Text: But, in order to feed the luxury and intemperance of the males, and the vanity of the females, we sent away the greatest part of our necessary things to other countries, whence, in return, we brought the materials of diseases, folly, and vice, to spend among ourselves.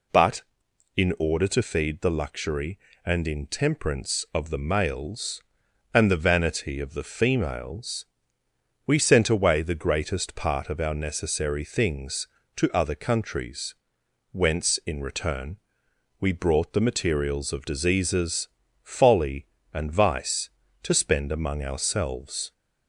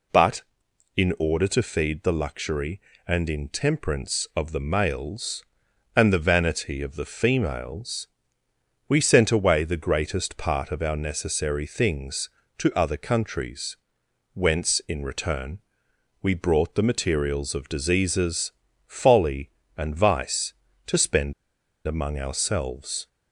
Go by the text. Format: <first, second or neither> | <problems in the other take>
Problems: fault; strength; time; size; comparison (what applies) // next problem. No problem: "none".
first | pauses between "spend" and "among"; noticeable; at 21.3 s; 0.54 s long